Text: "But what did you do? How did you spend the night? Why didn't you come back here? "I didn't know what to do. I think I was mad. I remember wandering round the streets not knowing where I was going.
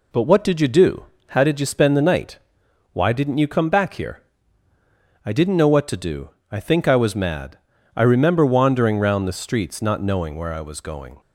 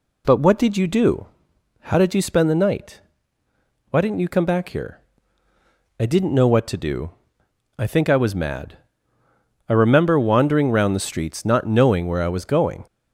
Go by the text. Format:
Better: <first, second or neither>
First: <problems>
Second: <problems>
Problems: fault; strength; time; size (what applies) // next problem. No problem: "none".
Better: neither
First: none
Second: none